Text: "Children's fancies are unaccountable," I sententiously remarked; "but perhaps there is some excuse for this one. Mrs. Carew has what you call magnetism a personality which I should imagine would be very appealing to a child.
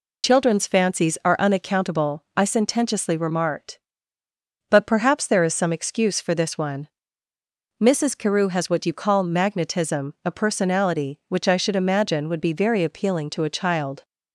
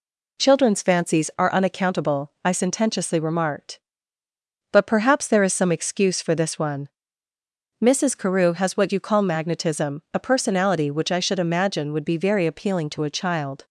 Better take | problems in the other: second | loses the start of "Children's"; at 0.2 s; 40 ms

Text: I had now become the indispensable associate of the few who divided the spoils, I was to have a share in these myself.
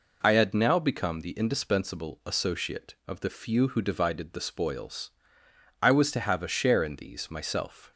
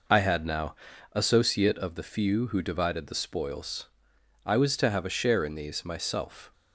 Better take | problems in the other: first | skips "become the indispensable"; at 0.9 s

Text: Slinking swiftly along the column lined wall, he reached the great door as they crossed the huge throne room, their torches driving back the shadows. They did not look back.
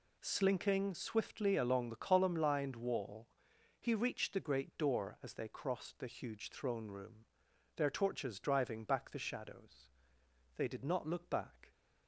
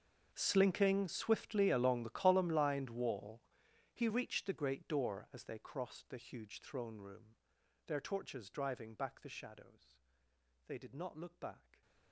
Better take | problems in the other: first | gets quieter; strong; throughout; 22 dB

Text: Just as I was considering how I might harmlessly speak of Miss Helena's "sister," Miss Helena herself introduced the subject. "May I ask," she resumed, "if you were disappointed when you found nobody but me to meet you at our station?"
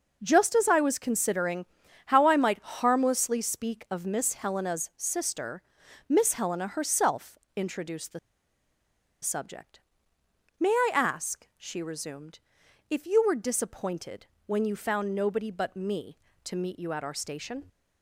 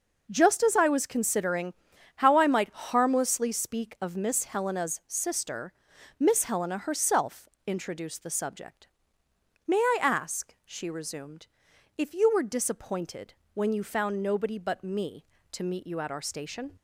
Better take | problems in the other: second | pauses between "considering" and "how"; at 1.6 s; 0.40 s long; also in the second // pauses between "herself" and "introduced"; slight; at 7.3 s; 0.18 s long; slight in the second // pauses between "the" and "subject"; at 8.1 s; 1.0 s long // pauses between "disappointed" and "when"; slight; at 14.2 s; 0.18 s long; slight in the second

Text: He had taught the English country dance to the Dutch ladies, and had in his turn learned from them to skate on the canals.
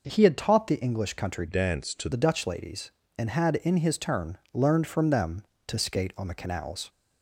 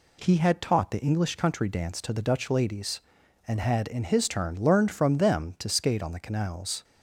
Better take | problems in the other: second | changes voice from "dance" to "to"; from 1.4 to 2.0 s; 0.6 s long // pauses between "turn" and "learned"; slight; at 4.3 s; 0.16 s long

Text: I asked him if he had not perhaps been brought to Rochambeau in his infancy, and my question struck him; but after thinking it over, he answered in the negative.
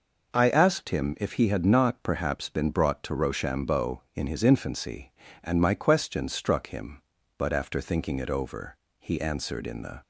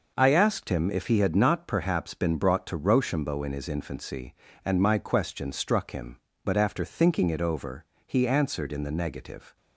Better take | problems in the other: second | stops before "negative"; at 10.0 s

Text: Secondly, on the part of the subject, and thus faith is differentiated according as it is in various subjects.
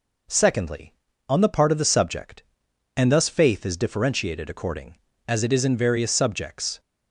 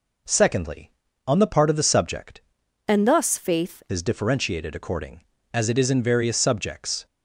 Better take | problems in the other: first | changes voice from "and" to "faith"; from 2.8 to 3.8 s; 1.0 s long

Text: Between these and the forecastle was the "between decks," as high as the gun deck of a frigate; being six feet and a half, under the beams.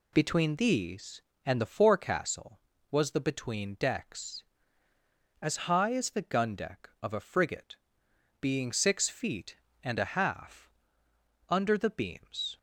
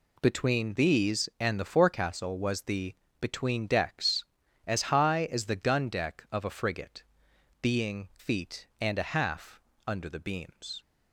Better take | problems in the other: first | pauses between "the" and "between"; slight; at 2.9 s; 0.24 s long // skips "six"; at 8.1 s

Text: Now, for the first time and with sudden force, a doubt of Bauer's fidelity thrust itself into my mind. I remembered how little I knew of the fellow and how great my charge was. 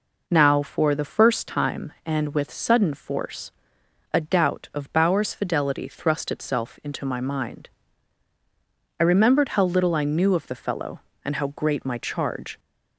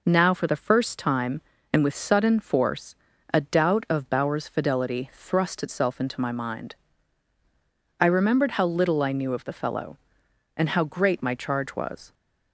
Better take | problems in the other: second | stops before "was"; at 12.5 s

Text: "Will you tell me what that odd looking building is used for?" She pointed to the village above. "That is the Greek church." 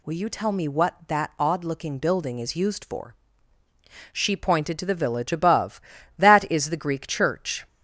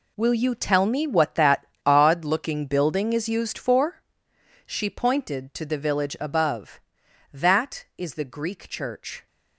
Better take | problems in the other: first | gets quieter; strong; throughout; 12 dB // pauses between "that" and "odd"; slight; at 1.6 s; 0.18 s long

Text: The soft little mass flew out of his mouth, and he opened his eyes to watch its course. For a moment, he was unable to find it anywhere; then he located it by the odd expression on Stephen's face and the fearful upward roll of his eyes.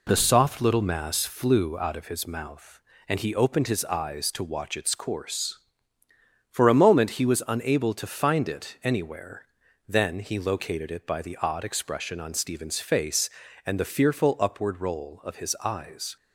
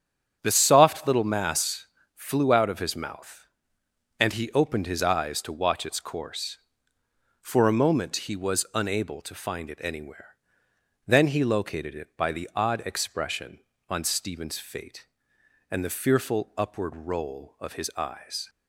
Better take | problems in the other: first | starts louder than the rest; strong; until 1.4 s; 8.5 dB // pauses between "mass" and "flew"; slight; at 1.8 s; 0.28 s long // says "fate" for "face"; at 14.5 s

